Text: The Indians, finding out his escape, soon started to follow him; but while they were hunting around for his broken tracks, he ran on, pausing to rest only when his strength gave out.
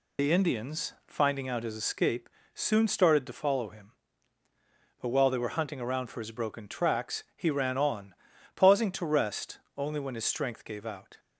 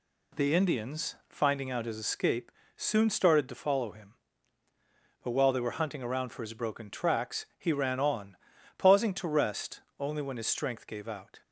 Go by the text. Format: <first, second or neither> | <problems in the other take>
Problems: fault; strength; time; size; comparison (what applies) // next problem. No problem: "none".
second | loses the start of "The"; at 0.1 s; 90 ms // pauses between "rest" and "only"; slight; at 9.5 s; 0.18 s long; slight in the second